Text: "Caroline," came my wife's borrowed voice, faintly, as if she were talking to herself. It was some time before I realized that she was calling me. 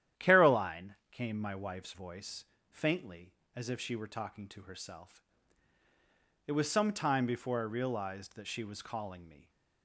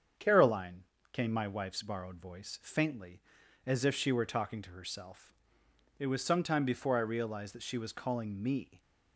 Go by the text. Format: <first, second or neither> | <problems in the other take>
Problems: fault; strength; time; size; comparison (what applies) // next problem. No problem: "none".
second | starts louder than the rest; strong; until 1.3 s; 11 dB; strong in the second // skips "borrowed"; at 1.9 s